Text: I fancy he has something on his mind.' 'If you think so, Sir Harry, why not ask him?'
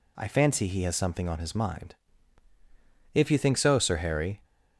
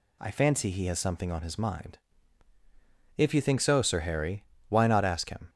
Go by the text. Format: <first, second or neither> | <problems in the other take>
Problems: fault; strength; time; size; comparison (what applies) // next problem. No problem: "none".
second | stops before "why not ask him"; at 4.4 s